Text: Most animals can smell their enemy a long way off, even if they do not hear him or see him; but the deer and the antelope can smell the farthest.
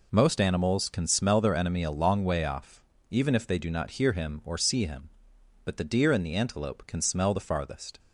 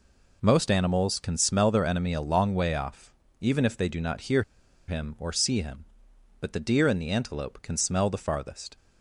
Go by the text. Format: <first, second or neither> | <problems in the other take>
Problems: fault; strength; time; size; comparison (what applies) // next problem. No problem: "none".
first | pauses between "hear" and "him"; at 4.4 s; 0.44 s long